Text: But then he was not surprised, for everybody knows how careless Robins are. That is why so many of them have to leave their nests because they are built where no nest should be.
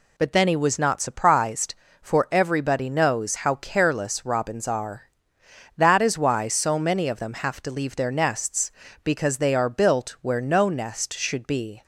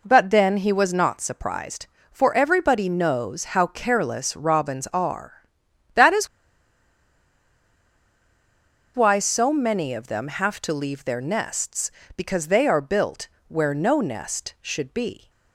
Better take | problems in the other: first | pauses between "is" and "why"; strong; at 6.2 s; 2.6 s long // pauses between "built" and "where"; slight; at 13.2 s; 0.20 s long

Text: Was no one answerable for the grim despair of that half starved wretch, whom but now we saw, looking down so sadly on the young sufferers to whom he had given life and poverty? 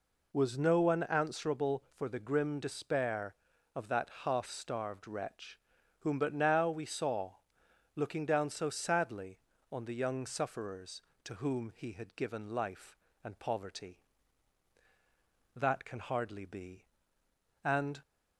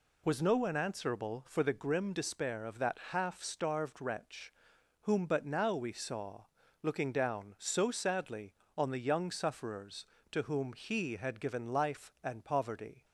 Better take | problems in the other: second | goes on to say "That can hardly be And"; strong; from 15.5 s on; 2.4 s long

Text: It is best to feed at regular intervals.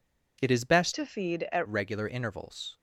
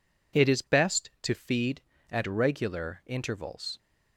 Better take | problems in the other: second | changes voice from "to" to "at"; from 0.9 to 1.6 s; 0.7 s long

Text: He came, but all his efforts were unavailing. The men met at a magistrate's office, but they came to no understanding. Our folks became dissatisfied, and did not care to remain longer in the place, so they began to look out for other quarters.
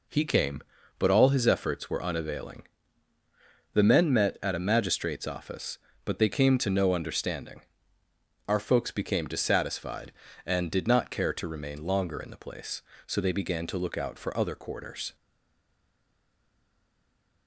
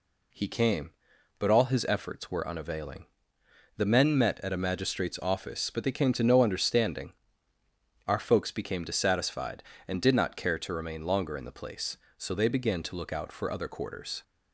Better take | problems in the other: second | stays silent after the last word; from 15.1 s on; 2.3 s long

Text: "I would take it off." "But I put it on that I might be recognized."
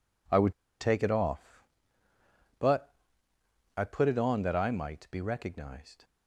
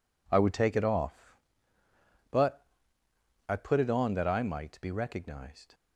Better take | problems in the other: second | pauses between "would" and "take"; slight; at 0.5 s; 0.28 s long // pauses between "But" and "I"; noticeable; at 2.9 s; 0.84 s long; noticeable in the second

